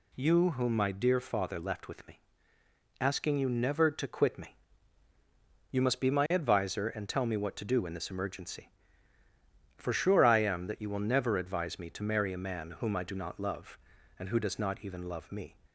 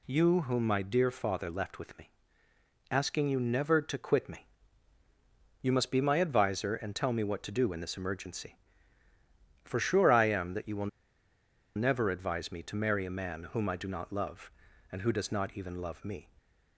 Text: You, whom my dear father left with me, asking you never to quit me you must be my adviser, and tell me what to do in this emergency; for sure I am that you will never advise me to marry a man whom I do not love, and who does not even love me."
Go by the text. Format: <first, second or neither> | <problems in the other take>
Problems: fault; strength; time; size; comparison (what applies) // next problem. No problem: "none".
first | pauses between "me" and "you"; at 4.4 s; 1.1 s long; also in the first // pauses between "will" and "never"; noticeable; at 10.8 s; 0.88 s long